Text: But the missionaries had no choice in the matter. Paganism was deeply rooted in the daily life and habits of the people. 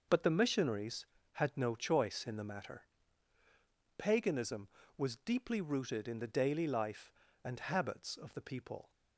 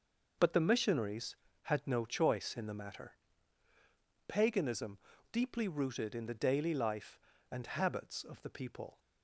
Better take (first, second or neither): first